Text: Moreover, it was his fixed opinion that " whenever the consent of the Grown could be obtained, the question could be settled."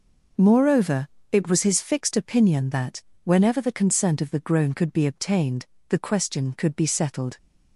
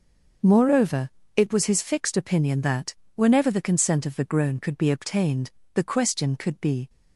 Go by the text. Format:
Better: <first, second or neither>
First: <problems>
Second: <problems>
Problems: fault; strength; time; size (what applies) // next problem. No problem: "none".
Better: first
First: none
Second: stops before "settled"; at 6.8 s